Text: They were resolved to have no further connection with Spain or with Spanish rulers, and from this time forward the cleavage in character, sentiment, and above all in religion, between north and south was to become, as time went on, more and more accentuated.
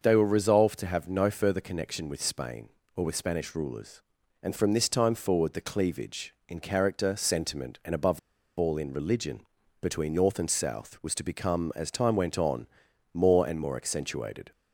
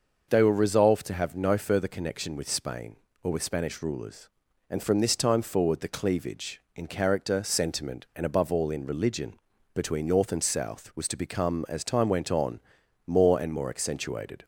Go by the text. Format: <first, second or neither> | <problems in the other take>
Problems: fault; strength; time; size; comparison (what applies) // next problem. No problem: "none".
second | starts louder than the rest; noticeable; until 1.0 s; 6 dB; noticeable in the second // pauses between "above" and "all"; at 8.1 s; 0.38 s long